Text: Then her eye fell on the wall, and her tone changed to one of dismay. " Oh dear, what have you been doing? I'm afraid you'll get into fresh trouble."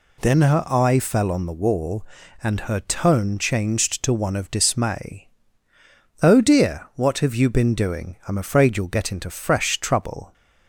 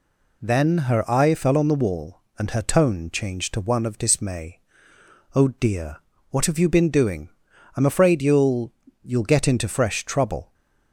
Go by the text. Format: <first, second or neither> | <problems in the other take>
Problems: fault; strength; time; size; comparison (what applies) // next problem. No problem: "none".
first | says "you'll" twice; at 9.0 s